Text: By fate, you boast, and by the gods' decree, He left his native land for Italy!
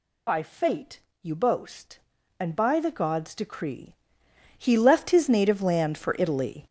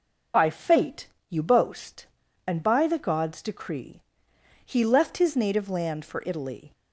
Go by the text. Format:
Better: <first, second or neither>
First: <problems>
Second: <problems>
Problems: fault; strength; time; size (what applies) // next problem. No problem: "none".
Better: second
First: gets louder; strong; throughout; 9 dB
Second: none